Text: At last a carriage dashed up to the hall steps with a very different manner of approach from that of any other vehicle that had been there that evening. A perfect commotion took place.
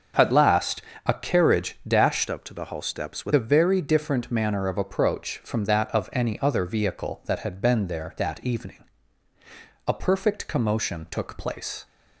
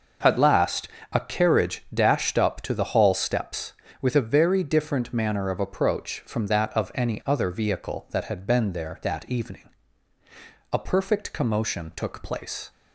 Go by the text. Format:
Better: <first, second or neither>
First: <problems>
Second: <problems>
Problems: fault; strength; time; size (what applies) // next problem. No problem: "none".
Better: second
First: starts louder than the rest; until 1.4 s; 6.5 dB // pauses between "last" and "a"; slight; at 0.8 s; 0.24 s long // changes voice from "up" to "with"; from 2.2 to 3.3 s; 1.1 s long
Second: starts louder than the rest; noticeable; until 1.4 s; 6 dB // pauses between "last" and "a"; slight; at 0.8 s; 0.24 s long